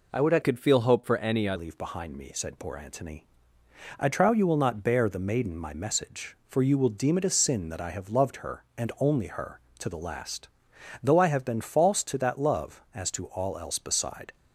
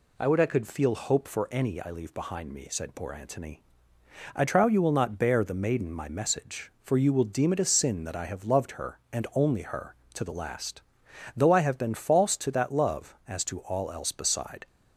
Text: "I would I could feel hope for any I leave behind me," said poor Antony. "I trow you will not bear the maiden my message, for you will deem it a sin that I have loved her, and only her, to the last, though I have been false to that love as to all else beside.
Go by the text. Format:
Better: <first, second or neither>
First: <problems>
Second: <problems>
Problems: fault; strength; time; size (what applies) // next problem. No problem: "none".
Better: second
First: changes voice from "could" to "I"; from 0.4 to 1.5 s; 1.1 s long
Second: none